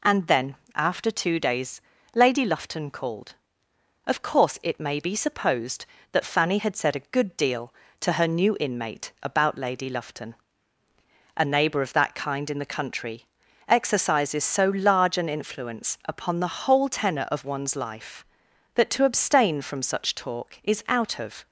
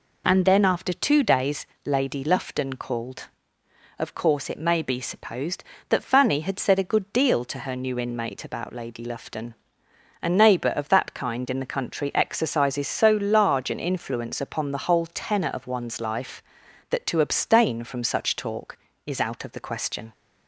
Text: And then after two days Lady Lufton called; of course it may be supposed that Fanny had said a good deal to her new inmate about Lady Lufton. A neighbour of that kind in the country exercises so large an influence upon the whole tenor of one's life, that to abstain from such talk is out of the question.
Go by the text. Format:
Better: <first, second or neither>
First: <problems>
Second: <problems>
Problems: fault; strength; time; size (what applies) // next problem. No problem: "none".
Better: second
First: pauses between "then" and "after"; slight; at 0.5 s; 0.18 s long // pauses between "days" and "Lady"; slight; at 1.8 s; 0.34 s long // pauses between "country" and "exercises"; at 13.2 s; 0.42 s long // stops before "the question"; at 21.4 s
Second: pauses between "days" and "Lady"; slight; at 1.6 s; 0.18 s long